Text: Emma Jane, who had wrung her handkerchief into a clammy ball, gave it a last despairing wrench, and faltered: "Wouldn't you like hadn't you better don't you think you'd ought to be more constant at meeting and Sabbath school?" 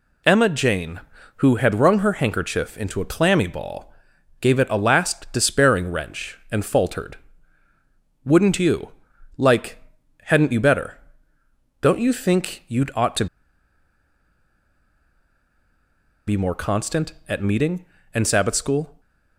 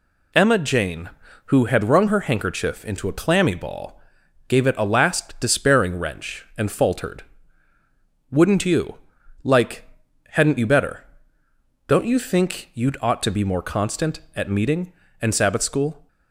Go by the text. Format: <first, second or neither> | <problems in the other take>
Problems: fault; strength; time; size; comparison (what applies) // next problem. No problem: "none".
second | pauses between "you" and "like"; noticeable; at 8.9 s; 0.46 s long; noticeable in the second // pauses between "like" and "hadn't"; noticeable; at 9.7 s; 0.46 s long; noticeable in the second // pauses between "better" and "don't"; noticeable; at 10.9 s; 0.82 s long; noticeable in the second // pauses between "to" and "be"; strong; at 13.2 s; 3.0 s long